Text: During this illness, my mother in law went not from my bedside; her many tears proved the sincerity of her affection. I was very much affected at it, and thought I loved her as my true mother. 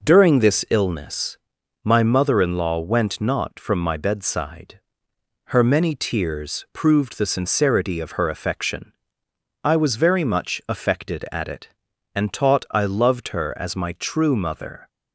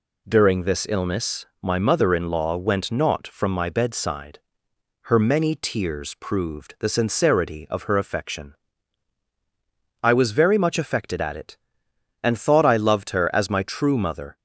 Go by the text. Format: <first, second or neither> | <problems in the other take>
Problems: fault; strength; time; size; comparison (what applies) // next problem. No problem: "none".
second | says "taught" for "thought"; at 12.3 s